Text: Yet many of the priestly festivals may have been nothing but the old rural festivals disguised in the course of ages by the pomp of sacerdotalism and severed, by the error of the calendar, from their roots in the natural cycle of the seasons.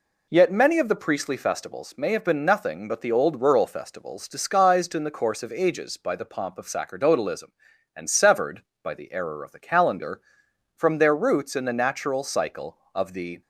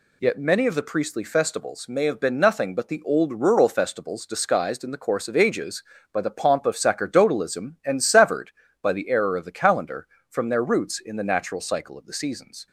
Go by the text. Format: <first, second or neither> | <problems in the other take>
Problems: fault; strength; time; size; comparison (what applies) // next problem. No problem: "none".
second | stops before "seasons"; at 13.4 s